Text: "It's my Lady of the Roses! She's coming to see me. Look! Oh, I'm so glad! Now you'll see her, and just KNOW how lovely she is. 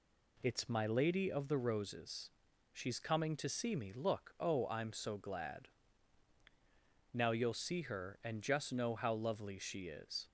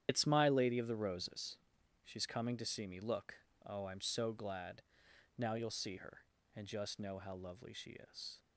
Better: first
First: none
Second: loses the start of "It's"; at 0.0 s; 105 ms // starts louder than the rest; strong; until 1.0 s; 10 dB

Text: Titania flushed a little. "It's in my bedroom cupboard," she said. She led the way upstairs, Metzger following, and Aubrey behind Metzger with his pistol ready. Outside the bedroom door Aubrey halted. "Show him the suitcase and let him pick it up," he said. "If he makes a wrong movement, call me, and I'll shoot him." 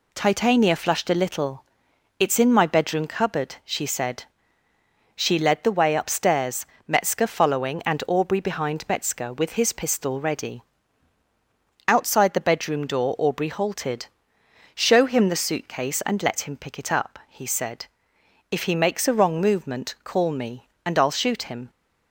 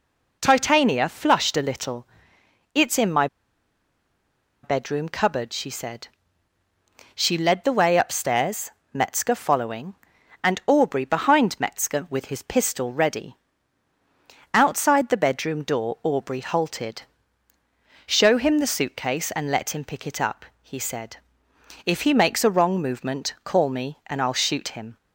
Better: first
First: none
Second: pauses between "my" and "bedroom"; strong; at 3.2 s; 1.3 s long

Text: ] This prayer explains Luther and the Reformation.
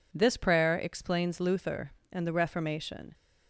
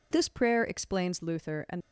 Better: first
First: none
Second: stops before "the Reformation"; at 1.7 s

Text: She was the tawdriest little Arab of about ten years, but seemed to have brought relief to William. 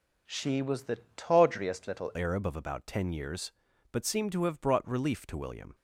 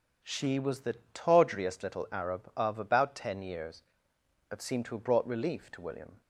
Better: second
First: pauses between "the" and "tawdriest"; slight; at 0.9 s; 0.20 s long // changes voice at "Arab"; from 2.1 s on; 3.6 s long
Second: pauses between "the" and "tawdriest"; slight; at 0.9 s; 0.20 s long

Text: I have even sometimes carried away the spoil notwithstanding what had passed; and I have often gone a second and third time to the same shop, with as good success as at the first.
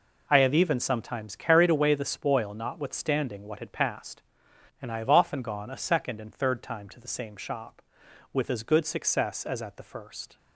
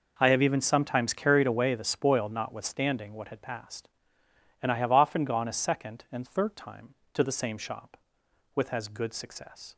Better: first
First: none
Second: stops before "as at the first"; at 9.7 s

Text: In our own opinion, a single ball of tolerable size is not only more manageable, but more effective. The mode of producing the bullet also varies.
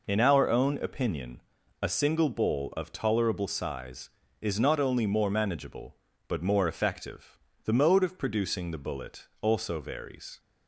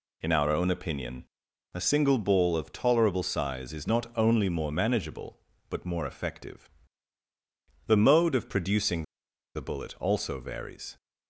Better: first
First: none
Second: pauses between "producing" and "the"; noticeable; at 9.0 s; 0.52 s long

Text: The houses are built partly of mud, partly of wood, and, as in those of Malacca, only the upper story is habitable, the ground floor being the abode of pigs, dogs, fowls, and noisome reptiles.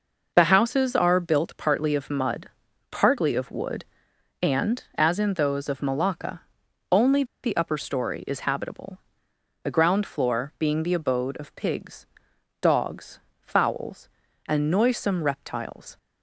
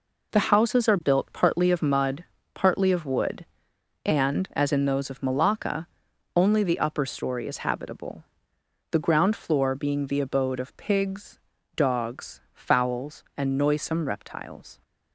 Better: second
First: pauses between "only" and "the"; slight; at 7.2 s; 0.21 s long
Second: none

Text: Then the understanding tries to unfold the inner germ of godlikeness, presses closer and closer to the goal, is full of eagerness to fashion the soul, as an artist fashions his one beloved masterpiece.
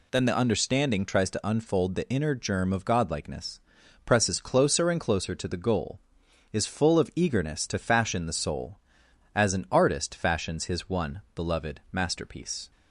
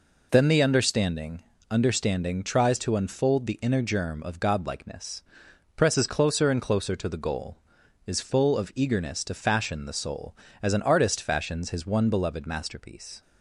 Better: first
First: none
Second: says "understanding" twice; at 1.7 s

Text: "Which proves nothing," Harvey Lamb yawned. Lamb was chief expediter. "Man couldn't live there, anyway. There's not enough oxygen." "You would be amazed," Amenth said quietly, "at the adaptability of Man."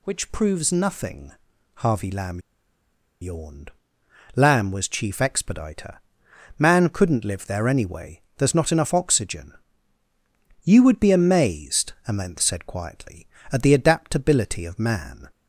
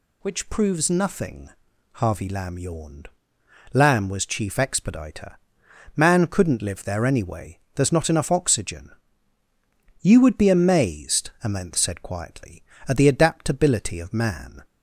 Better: second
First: pauses between "Lamb" and "yawned"; noticeable; at 2.4 s; 0.80 s long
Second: none

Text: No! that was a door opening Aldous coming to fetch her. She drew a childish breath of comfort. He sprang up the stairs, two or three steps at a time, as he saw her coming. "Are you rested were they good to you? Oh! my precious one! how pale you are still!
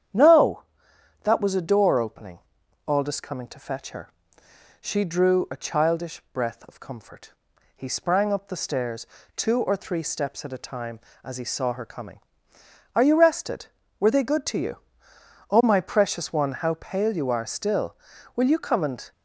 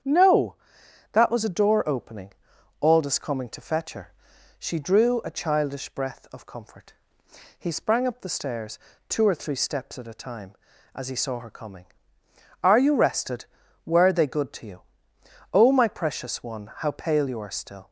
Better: second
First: starts louder than the rest; strong; until 1.7 s; 9 dB // pauses between "opening" and "Aldous"; noticeable; at 2.3 s; 0.50 s long // goes on to say "Will you come and"; noticeable; from 18.3 s on; 0.76 s long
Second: starts louder than the rest; strong; until 1.6 s; 8 dB // pauses between "opening" and "Aldous"; noticeable; at 2.3 s; 0.48 s long

